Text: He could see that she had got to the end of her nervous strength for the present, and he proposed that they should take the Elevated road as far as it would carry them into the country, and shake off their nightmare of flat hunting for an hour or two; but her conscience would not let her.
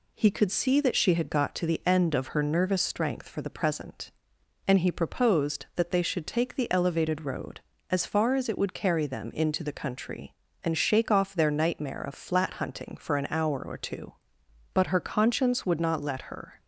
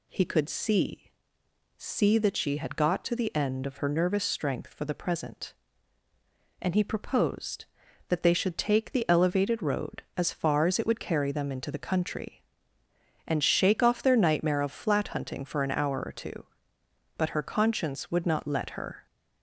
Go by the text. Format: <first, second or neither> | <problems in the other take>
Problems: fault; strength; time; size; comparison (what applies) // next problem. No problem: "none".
first | says "see" twice; at 1.8 s